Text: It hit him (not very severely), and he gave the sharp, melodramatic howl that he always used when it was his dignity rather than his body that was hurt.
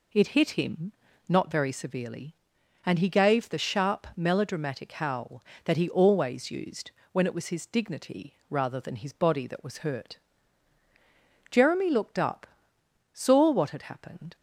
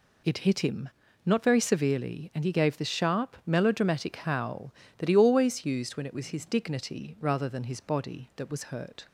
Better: second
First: pauses between "used" and "when"; slight; at 6.8 s; 0.22 s long // goes on to say "Jeremy looked up saw what had happened"; strong; from 11.5 s on; 2.8 s long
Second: none

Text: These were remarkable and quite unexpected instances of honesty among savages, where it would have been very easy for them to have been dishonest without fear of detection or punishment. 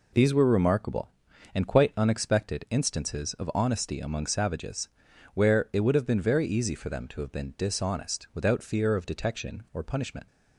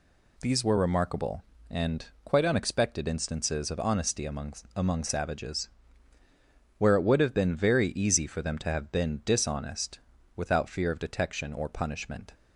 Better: first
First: none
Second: pauses between "and" and "quite"; slight; at 2.0 s; 0.20 s long // says "among" twice; at 4.7 s // pauses between "dishonest" and "without"; slight; at 9.9 s; 0.36 s long

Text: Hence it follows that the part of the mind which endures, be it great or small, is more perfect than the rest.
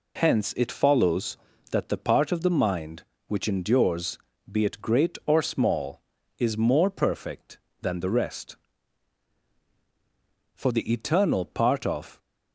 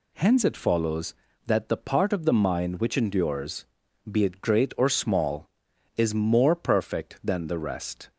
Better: second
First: goes on to say "For the eternal part of"; from 10.5 s on; 1.6 s long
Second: none

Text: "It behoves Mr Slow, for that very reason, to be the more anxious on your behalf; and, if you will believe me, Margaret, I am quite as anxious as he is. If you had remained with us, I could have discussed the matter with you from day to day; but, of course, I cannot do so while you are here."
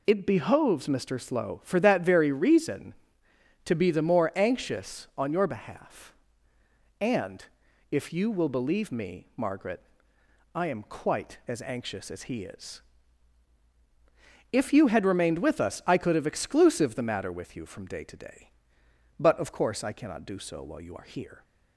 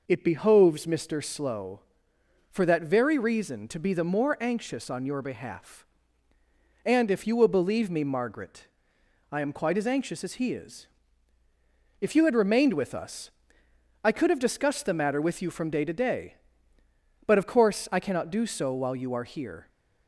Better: second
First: says "exclusive" for "discussed"; at 16.2 s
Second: none

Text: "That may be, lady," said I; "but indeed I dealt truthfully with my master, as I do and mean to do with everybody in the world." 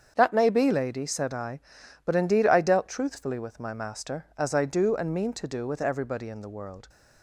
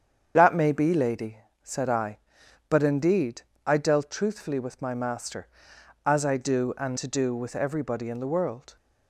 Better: first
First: starts louder than the rest; strong; until 1.1 s; 7.5 dB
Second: starts louder than the rest; strong; until 1.3 s; 8 dB // pauses between "indeed" and "I"; slight; at 3.4 s; 0.26 s long // skips "mean"; at 6.9 s

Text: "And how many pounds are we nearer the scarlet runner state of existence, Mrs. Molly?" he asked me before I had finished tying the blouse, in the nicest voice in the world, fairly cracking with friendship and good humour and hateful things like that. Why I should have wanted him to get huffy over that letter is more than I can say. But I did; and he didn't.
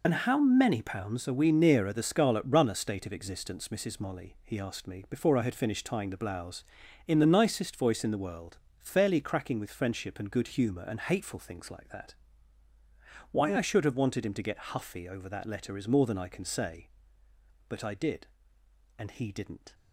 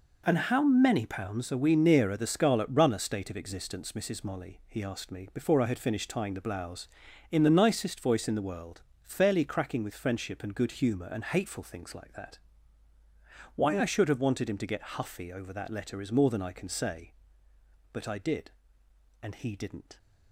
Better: second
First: loses the start of "And"; at 0.0 s; 35 ms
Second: none

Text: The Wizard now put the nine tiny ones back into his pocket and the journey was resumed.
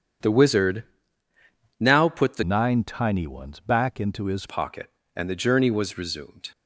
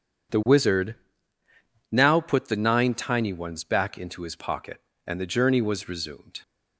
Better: second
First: starts louder than the rest; strong; until 2.1 s; 8 dB // pauses between "Wizard" and "now"; noticeable; at 0.8 s; 0.96 s long // changes voice from "nine" to "his"; from 2.4 to 4.4 s; 2.0 s long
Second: pauses between "Wizard" and "now"; noticeable; at 0.9 s; 0.96 s long

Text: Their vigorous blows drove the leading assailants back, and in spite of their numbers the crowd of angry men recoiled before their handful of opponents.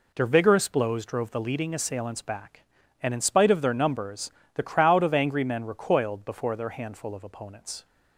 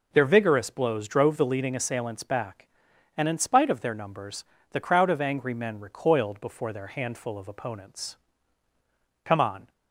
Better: first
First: pauses between "numbers" and "the"; slight; at 4.3 s; 0.24 s long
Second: pauses between "numbers" and "the"; slight; at 4.4 s; 0.28 s long // goes on to say "Come on"; slight; from 9.2 s on; 0.48 s long

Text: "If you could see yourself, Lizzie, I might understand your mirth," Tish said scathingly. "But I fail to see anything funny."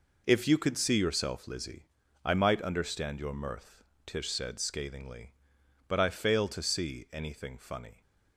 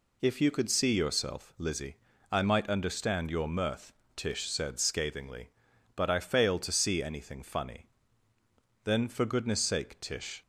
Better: first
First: none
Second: goes on to say "Then for goodness sake Tish"; from 8.8 s on; 1.5 s long

